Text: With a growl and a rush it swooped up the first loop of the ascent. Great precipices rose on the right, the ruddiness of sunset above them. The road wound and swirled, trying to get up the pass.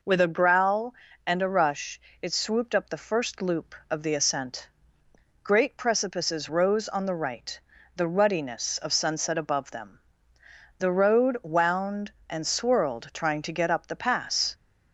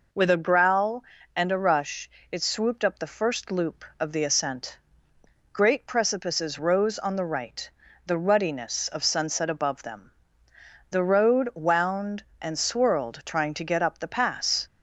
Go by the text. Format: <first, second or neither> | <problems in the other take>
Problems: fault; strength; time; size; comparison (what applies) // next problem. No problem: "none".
neither | pauses between "rush" and "it"; slight; the same in both